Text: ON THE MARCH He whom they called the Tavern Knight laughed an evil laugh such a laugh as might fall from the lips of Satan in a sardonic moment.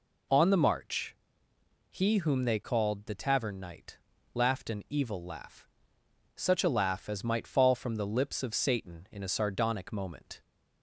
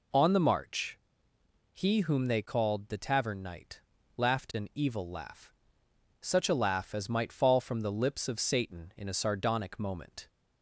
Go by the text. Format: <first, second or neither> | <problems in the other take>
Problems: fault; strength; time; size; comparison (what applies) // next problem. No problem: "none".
neither | pauses between "MARCH" and "He"; noticeable; the same in both // pauses between "Knight" and "laughed"; slight; the same in both // pauses between "laugh" and "such"; noticeable; the same in both